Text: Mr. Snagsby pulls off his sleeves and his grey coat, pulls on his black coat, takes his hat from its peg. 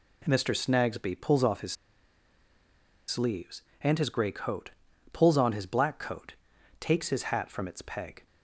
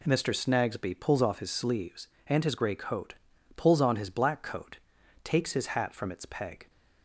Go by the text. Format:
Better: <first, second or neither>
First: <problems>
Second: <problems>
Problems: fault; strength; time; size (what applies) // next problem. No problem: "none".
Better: second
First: pauses between "his" and "sleeves"; strong; at 1.7 s; 1.3 s long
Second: none